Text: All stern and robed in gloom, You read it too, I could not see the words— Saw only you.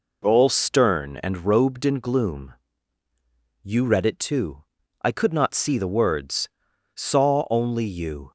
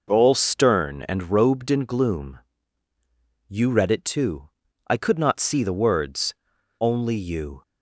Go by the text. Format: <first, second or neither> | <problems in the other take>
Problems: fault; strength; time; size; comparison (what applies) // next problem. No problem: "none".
first | skips "Saw"; at 6.5 s